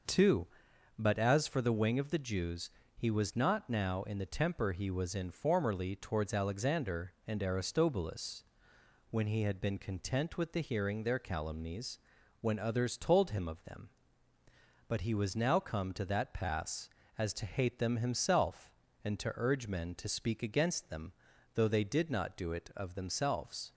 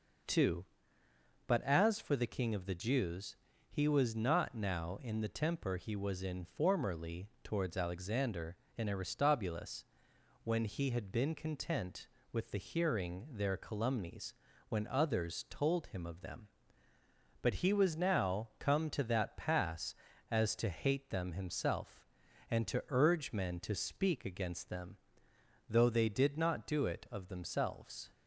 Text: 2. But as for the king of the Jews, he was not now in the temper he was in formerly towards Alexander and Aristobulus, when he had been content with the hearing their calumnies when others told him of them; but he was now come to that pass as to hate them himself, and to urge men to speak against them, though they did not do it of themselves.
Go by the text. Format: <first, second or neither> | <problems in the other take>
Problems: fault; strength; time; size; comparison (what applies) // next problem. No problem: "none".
second | says "wing" for "king"; at 1.7 s // pauses between "calumnies" and "when"; at 11.9 s; 0.42 s long; slight in the second